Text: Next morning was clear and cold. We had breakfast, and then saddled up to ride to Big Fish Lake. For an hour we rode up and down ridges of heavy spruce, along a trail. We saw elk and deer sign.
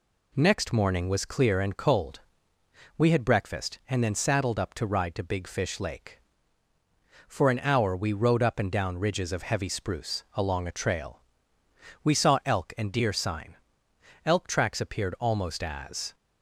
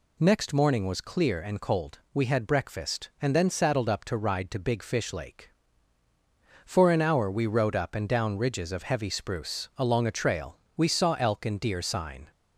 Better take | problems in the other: second | goes on to say "Elk tracks appeared almost as"; strong; from 14.2 s on; 1.9 s long

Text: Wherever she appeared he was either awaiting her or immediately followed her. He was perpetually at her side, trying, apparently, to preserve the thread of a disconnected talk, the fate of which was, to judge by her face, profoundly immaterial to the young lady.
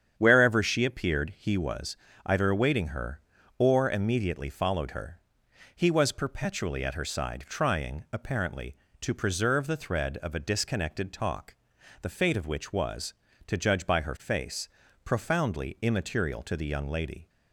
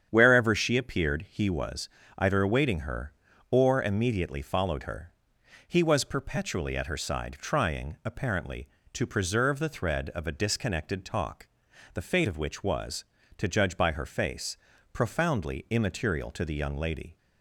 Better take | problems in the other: neither | starts louder than the rest; strong; the same in both // pauses between "was" and "either"; slight; the same in both

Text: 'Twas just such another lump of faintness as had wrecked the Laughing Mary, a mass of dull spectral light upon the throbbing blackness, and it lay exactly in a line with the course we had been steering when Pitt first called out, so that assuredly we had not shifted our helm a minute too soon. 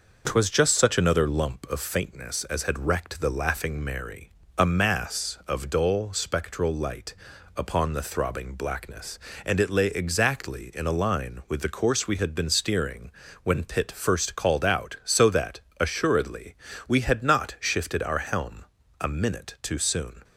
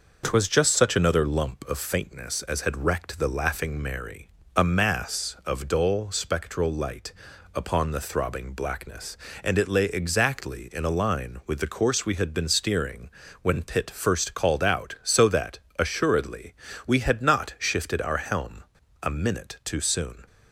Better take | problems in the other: neither | pauses between "light" and "upon"; the same in both // pauses between "steering" and "when"; slight; the same in both // pauses between "that" and "assuredly"; slight; the same in both // pauses between "assuredly" and "we"; slight; the same in both // pauses between "helm" and "a"; the same in both

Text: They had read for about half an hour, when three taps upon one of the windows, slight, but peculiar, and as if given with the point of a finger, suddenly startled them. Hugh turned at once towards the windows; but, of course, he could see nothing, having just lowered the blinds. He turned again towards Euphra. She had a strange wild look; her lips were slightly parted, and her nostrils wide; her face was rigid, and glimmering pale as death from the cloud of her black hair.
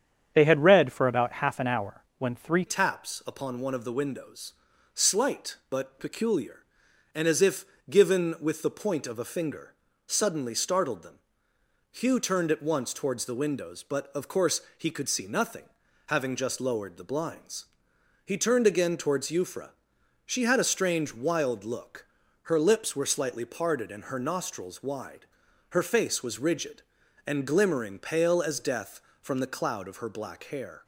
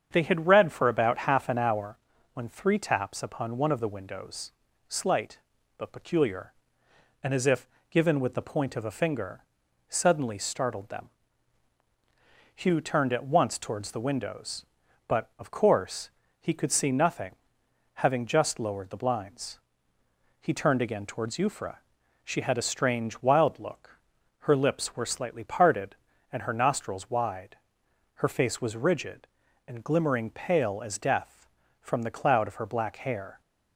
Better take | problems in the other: second | starts louder than the rest; strong; until 1.3 s; 8 dB; strong in the second // changes voice at "taps"; from 2.6 s on; 28.2 s long // pauses between "if" and "given"; slight; at 7.6 s; 0.24 s long; slight in the second

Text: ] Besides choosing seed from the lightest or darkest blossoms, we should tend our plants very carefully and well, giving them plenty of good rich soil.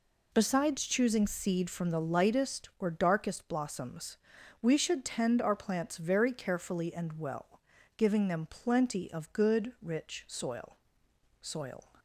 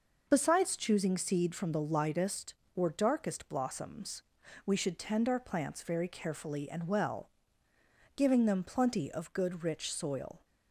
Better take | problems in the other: second | says "soil" twice; at 11.4 s

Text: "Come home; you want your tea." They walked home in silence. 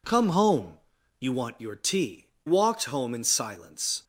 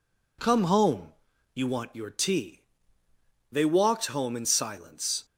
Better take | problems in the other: second | skips "They"; at 2.3 s

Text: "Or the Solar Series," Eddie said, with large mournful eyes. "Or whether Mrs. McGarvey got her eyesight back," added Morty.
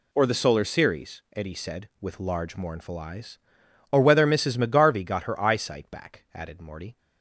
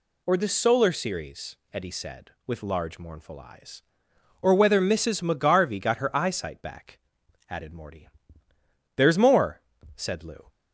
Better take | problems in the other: first | goes on to say "There's more said Lou"; from 8.9 s on; 1.5 s long

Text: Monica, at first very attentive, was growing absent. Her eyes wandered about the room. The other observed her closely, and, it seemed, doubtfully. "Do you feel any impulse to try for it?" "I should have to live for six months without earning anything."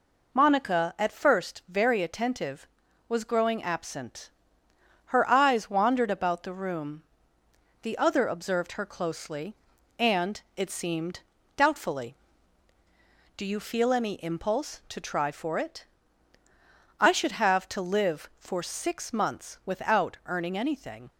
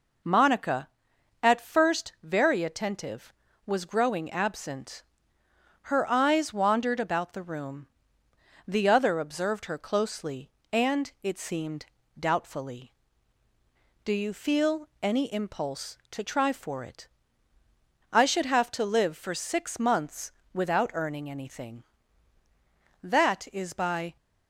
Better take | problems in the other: first | pauses between "months" and "without"; slight; at 20.3 s; 0.20 s long // goes on to say "That is by"; noticeable; from 23.0 s on; 1.1 s long

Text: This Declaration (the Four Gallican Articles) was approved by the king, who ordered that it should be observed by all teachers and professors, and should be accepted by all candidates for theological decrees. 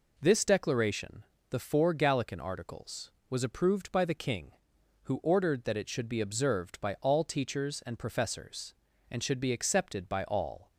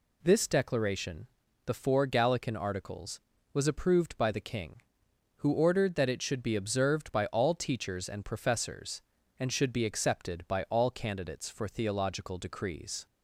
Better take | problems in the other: second | stops before "candidates for theological decrees"; at 10.7 s

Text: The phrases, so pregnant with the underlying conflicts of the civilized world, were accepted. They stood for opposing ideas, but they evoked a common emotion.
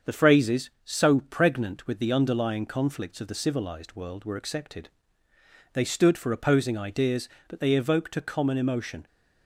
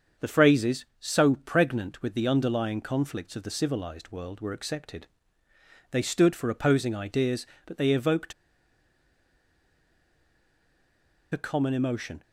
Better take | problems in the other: first | starts louder than the rest; until 1.3 s; 7 dB; also in the first // pauses between "evoked" and "a"; strong; at 8.3 s; 2.9 s long

